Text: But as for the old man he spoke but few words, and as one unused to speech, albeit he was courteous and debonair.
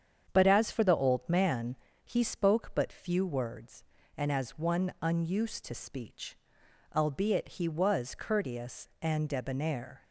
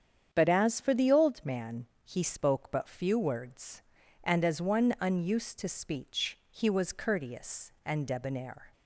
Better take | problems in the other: first | starts louder than the rest; strong; until 1.3 s; 8.5 dB; strong in the first // pauses between "man" and "he"; slight; at 1.8 s; 0.18 s long; slight in the first // skips "albeit"; at 6.4 s

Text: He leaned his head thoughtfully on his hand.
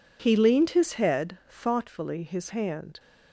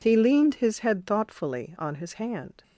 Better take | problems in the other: second | skips "on"; at 2.2 s

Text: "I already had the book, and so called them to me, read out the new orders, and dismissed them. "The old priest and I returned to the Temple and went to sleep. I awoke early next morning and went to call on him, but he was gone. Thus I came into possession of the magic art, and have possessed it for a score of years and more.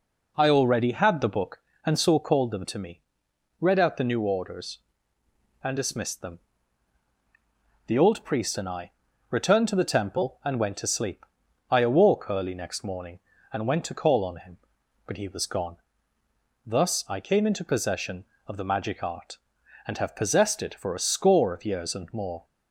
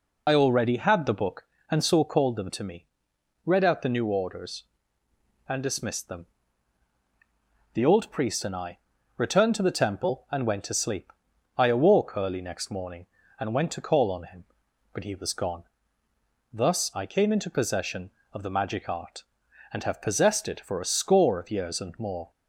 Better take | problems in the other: first | loses the start of "I"; at 0.2 s; 55 ms // pauses between "I" and "returned"; slight; at 8.7 s; 0.36 s long; slight in the first

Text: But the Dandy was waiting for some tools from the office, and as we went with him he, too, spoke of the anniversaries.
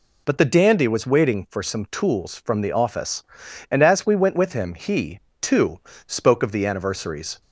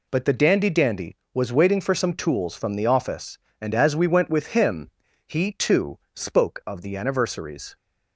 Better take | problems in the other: first | says "Dandy" twice; at 0.6 s // pauses between "him" and "he"; slight; at 4.8 s; 0.36 s long

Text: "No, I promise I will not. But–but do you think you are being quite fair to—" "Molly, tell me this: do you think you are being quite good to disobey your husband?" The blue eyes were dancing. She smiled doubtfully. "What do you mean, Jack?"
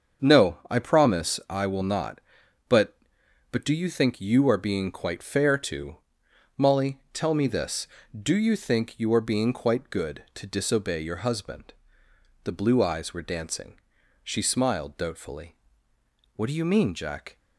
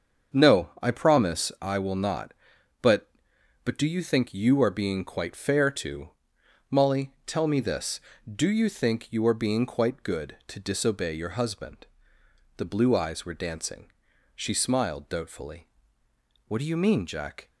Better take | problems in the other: neither | starts louder than the rest; the same in both

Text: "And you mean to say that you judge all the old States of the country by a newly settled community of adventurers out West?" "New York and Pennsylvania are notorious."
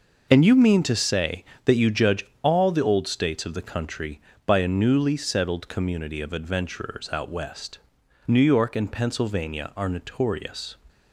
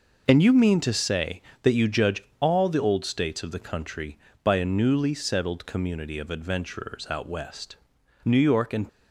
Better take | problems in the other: first | pauses between "judge" and "all"; slight; at 2.2 s; 0.16 s long; slight in the first // stops before "Pennsylvania are notorious"; at 8.8 s

